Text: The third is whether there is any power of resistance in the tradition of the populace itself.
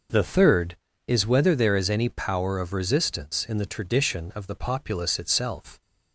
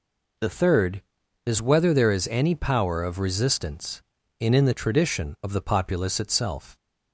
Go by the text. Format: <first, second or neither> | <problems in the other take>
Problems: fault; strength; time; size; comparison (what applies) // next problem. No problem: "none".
first | says "in" twice; at 4.5 s